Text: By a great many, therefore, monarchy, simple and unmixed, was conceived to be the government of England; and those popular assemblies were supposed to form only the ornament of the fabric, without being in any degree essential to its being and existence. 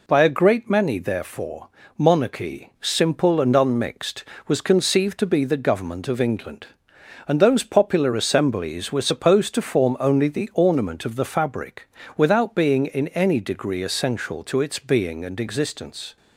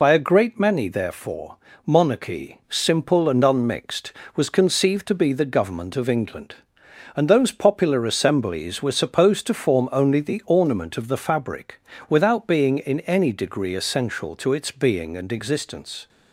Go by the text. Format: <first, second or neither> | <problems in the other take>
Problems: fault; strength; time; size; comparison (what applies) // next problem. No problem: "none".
first | loses the start of "By"; at 0.0 s; 30 ms